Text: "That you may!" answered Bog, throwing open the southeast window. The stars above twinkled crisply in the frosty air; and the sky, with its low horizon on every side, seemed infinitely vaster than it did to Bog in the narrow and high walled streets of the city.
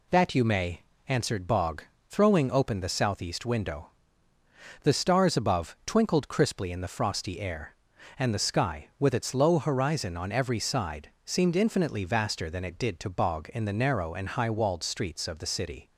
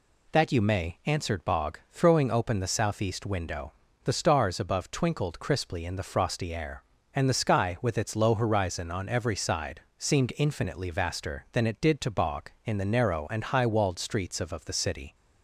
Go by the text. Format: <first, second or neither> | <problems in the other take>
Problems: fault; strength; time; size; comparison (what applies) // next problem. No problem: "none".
first | says "of" twice; at 14.5 s